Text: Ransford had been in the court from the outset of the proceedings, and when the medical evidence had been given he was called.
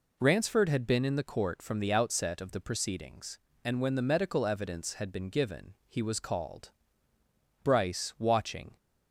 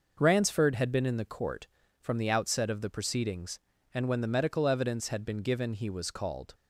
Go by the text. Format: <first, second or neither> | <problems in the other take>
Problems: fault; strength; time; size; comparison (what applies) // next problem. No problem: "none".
second | goes on to say "Bryce watching"; noticeable; from 7.6 s on; 1.1 s long